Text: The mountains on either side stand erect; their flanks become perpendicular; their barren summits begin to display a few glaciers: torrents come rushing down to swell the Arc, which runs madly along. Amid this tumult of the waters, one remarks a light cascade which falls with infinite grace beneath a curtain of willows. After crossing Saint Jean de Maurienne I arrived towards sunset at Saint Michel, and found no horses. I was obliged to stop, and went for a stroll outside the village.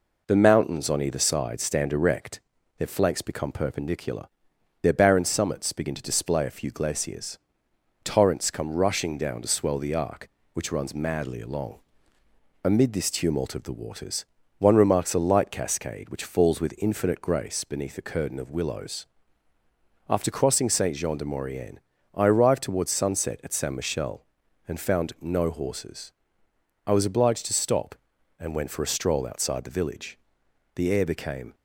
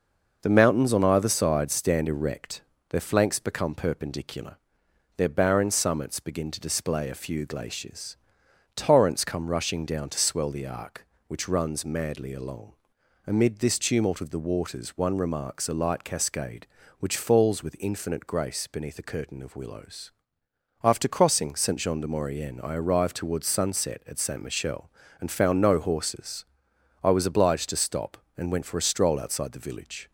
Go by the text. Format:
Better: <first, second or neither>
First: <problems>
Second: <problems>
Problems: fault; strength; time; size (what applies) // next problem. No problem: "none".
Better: second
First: pauses between "Maurienne" and "I"; slight; at 21.8 s; 0.34 s long // goes on to say "The air became"; noticeable; from 30.7 s on; 0.80 s long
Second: none